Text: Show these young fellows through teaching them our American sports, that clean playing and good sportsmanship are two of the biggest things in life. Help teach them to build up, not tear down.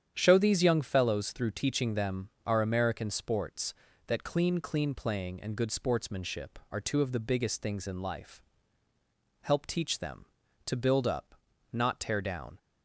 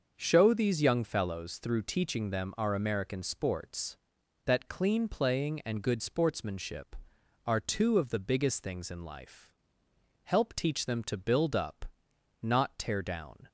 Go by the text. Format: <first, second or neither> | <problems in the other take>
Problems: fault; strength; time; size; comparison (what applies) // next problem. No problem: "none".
second | starts louder than the rest; strong; until 1.1 s; 9 dB; also in the second // pauses between "them" and "our"; slight; at 2.2 s; 0.18 s long // says "clean" twice; at 4.5 s